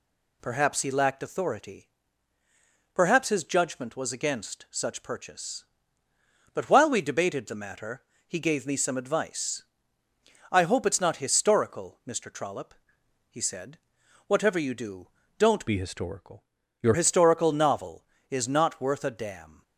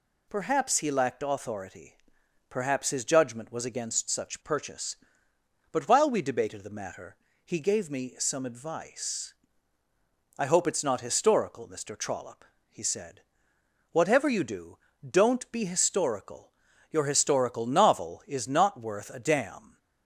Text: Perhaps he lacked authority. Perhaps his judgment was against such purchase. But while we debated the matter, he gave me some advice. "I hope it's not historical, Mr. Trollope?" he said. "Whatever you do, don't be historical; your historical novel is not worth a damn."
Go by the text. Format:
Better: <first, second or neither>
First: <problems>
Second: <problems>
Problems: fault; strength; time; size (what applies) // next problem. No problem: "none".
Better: second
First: changes voice from "be" to "your"; from 15.6 to 16.9 s; 1.3 s long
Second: none